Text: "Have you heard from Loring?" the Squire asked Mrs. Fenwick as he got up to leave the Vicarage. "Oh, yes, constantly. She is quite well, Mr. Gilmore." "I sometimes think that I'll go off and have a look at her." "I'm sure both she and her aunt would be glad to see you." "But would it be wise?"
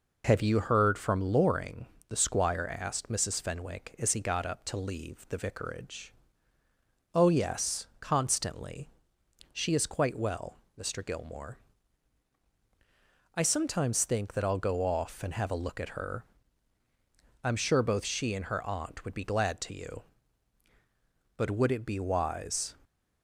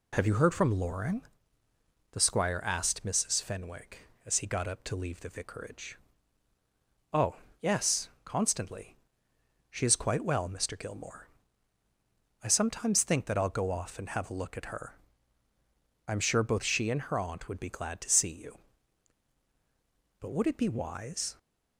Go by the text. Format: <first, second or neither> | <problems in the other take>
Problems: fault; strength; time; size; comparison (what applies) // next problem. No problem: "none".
second | skips "see"; at 19.7 s